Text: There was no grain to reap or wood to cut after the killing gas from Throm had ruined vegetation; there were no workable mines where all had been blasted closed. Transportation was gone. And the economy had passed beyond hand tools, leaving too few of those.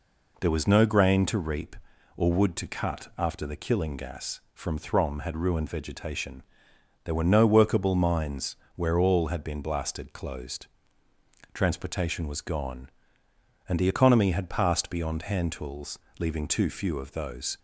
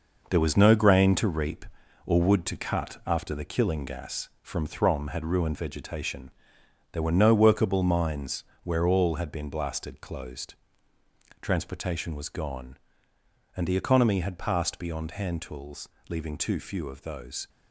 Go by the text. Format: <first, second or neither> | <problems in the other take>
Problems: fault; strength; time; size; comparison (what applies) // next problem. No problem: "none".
first | gets quieter; strong; throughout; 7 dB // pauses between "mines" and "where"; slight; at 8.4 s; 0.18 s long; slight in the first